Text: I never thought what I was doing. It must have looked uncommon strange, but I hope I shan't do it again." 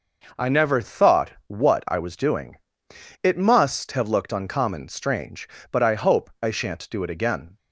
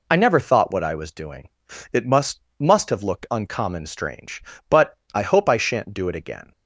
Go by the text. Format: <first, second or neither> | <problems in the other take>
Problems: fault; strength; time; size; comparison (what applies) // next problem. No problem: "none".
first | says "must" twice; at 2.5 s // pauses between "but" and "I"; slight; at 4.9 s; 0.16 s long